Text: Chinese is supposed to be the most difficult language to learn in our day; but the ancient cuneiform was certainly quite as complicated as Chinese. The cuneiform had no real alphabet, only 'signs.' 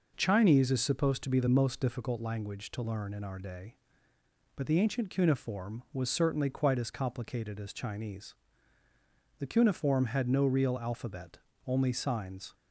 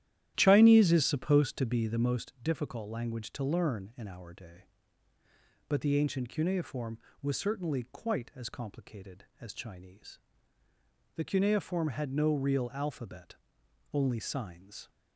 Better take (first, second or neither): first